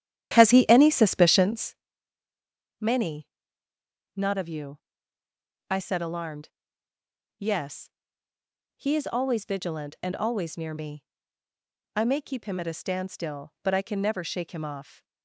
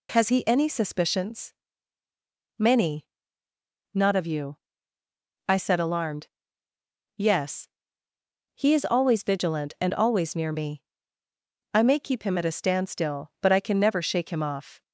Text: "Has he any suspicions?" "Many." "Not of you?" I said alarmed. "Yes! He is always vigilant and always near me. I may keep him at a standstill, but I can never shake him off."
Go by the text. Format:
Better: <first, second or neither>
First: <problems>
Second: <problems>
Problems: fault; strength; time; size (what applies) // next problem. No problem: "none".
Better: second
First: starts louder than the rest; strong; until 1.9 s; 11 dB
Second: none